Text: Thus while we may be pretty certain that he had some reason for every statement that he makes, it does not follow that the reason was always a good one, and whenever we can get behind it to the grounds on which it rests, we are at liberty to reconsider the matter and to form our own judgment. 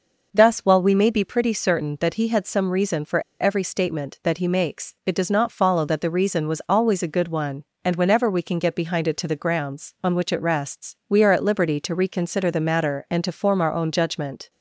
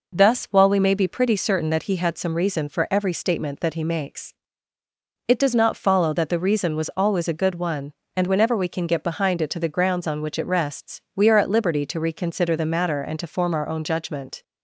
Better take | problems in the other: second | pauses between "for" and "every"; slight; at 3.2 s; 0.20 s long

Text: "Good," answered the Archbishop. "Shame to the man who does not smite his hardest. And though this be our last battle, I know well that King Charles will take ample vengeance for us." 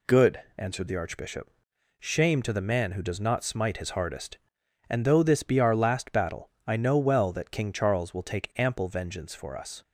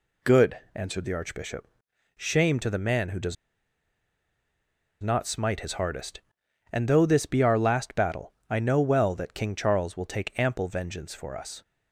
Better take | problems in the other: first | pauses between "does" and "not"; strong; at 3.3 s; 1.6 s long

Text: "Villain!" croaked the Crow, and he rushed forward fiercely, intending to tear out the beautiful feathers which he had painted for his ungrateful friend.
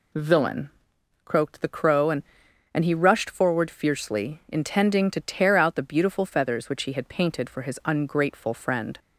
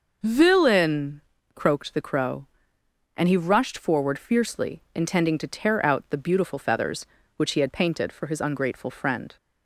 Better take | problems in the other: second | says "and" twice; at 2.7 s

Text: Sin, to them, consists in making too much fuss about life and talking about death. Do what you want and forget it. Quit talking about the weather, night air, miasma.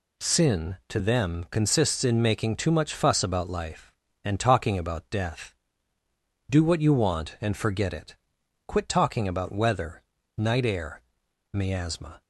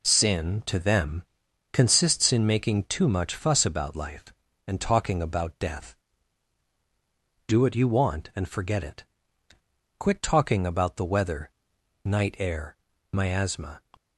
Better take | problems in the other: second | skips "the"; at 9.5 s

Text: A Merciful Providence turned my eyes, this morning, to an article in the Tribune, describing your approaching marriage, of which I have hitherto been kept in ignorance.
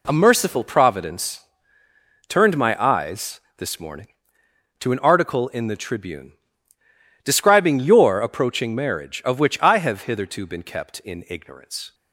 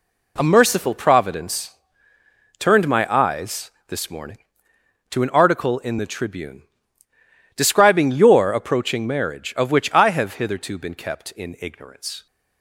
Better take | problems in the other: neither | pauses between "Providence" and "turned"; noticeable; the same in both

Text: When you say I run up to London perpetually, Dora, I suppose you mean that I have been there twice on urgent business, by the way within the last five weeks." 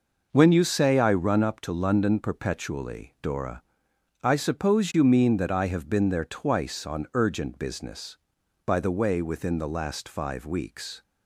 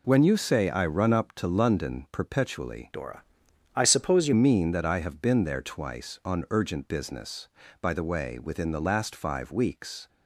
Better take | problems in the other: first | changes voice from "Dora" to "you"; from 2.9 to 4.3 s; 1.4 s long

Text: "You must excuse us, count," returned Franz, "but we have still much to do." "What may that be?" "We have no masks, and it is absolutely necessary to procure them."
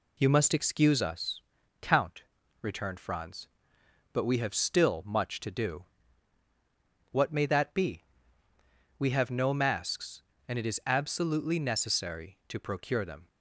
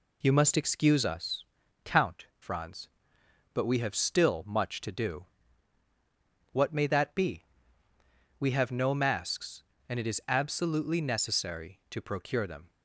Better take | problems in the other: first | skips "returned"; at 2.3 s

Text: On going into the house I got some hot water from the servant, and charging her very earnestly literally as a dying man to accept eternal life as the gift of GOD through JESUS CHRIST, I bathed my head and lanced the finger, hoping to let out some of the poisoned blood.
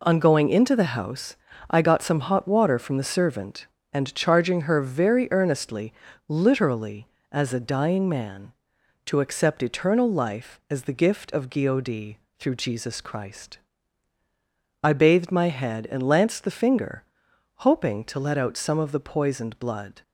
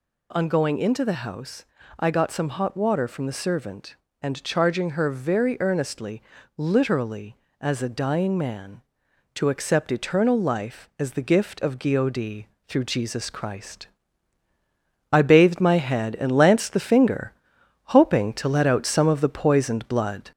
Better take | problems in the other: first | gets louder; slight; throughout; 2.5 dB // pauses between "house" and "I"; slight; at 1.6 s; 0.34 s long; slight in the first // pauses between "earnestly" and "literally"; slight; at 6.2 s; 0.34 s long; slight in the first // pauses between "GOD" and "through"; slight; at 12.4 s; 0.24 s long; slight in the first

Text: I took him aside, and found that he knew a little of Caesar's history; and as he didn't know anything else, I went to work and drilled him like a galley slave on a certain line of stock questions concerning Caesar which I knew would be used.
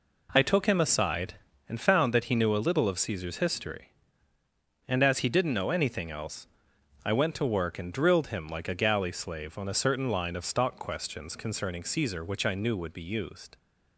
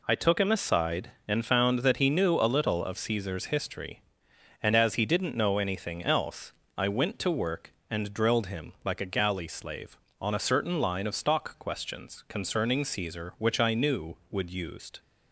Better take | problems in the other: first | skips "be"; at 14.4 s

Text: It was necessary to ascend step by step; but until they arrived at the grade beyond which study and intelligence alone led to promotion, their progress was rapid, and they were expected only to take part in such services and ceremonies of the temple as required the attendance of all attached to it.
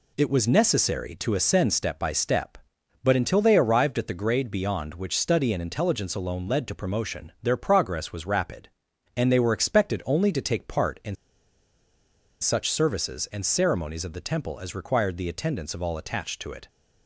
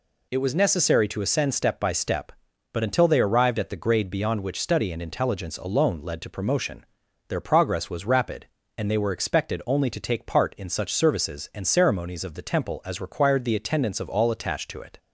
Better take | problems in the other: second | pauses between "in" and "such"; strong; at 11.1 s; 1.2 s long

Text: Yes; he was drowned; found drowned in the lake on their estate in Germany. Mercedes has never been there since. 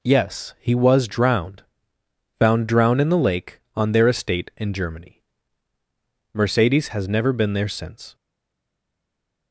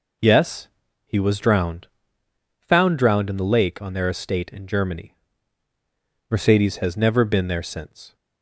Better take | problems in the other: second | stays silent after the last word; noticeable; from 8.1 s on; 1.4 s long

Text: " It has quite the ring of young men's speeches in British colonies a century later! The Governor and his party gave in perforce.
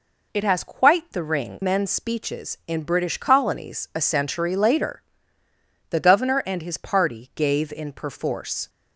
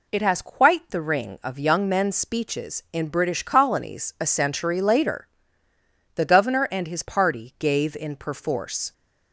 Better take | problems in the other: second | skips "of young"; at 1.6 s

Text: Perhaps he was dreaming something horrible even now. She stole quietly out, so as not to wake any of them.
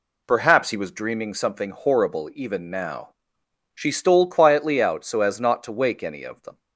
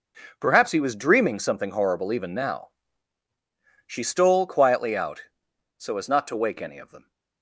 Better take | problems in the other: first | gets quieter; strong; throughout; 13 dB

